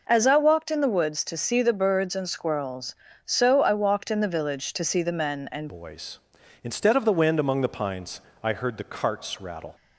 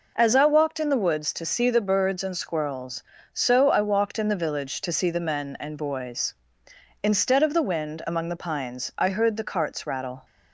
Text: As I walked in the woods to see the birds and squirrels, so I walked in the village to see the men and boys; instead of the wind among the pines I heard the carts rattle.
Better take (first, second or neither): second